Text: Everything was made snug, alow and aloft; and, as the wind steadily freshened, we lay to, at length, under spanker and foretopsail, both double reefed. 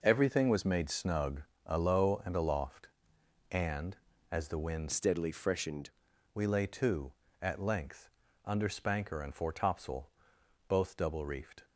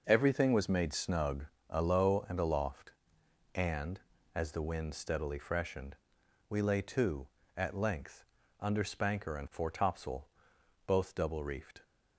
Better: second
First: changes voice from "steadily" to "freshened"; from 4.9 to 5.9 s; 1.0 s long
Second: none

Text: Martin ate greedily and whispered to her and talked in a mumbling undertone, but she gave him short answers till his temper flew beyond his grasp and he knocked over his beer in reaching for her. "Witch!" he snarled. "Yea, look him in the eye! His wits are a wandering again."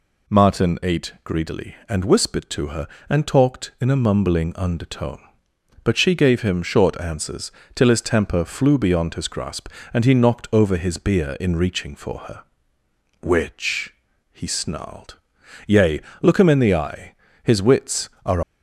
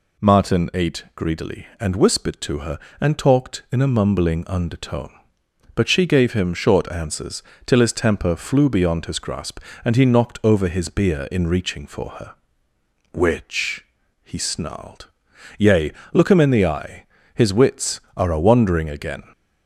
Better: second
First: pauses between "answers" and "till"; slight; at 7.5 s; 0.24 s long // stops before "a wandering again"; at 18.4 s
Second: pauses between "answers" and "till"; slight; at 7.4 s; 0.24 s long

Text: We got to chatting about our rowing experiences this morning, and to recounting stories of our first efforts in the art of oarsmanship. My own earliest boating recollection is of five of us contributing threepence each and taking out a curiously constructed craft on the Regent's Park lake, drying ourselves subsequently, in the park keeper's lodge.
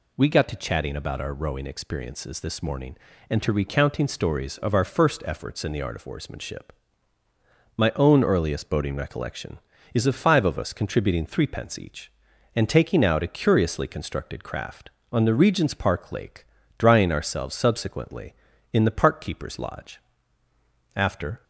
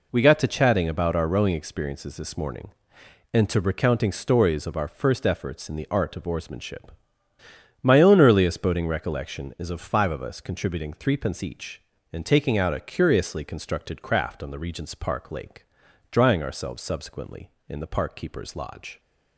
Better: second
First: goes on to say "After"; slight; from 20.9 s on; 0.48 s long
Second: none

